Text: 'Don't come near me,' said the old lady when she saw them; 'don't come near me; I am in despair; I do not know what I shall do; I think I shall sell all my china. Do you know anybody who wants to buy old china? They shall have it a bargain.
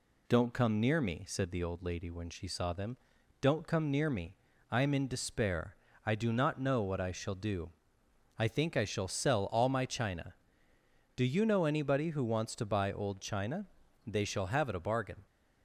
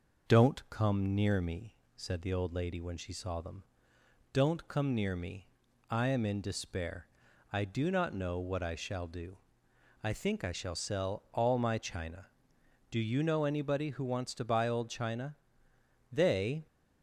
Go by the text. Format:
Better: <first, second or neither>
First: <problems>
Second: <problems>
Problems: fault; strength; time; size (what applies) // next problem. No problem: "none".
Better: first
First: none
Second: stops before "shall have it a bargain"; at 16.6 s